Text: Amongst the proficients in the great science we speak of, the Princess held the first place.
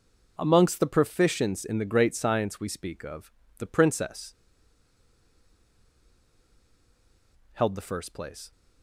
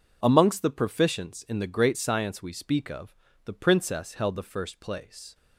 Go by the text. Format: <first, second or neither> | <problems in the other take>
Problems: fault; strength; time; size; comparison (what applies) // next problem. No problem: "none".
second | pauses between "Princess" and "held"; strong; at 4.3 s; 3.1 s long